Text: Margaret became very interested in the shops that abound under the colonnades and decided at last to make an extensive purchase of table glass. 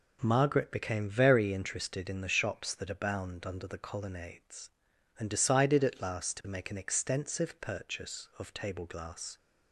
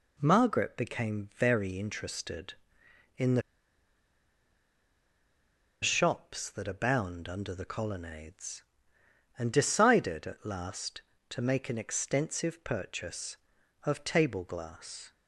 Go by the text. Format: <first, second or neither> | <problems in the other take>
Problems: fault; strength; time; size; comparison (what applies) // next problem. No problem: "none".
first | pauses between "the" and "shops"; strong; at 3.4 s; 2.4 s long